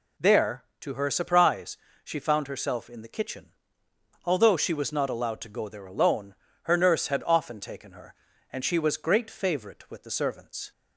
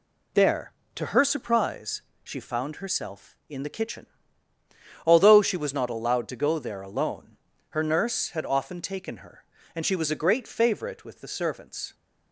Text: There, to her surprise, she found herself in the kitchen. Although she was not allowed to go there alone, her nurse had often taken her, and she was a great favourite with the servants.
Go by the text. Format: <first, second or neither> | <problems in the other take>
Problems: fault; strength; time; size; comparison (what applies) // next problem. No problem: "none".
second | skips "a"; at 8.9 s